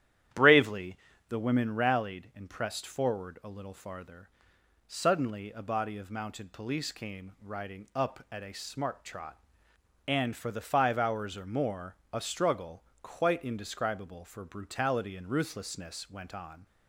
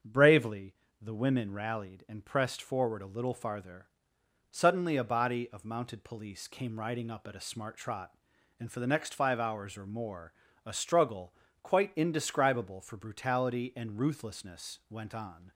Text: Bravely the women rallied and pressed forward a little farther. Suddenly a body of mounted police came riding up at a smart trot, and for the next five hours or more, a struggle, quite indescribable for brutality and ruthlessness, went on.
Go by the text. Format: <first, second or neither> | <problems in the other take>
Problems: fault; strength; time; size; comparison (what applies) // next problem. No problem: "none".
second | starts louder than the rest; strong; until 1.6 s; 11 dB; strong in the second // pauses between "Bravely" and "the"; slight; at 0.9 s; 0.32 s long; slight in the second // skips "next"; at 10.6 s